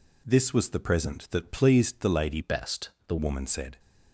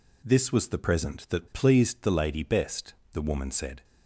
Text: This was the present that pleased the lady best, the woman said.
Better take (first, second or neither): second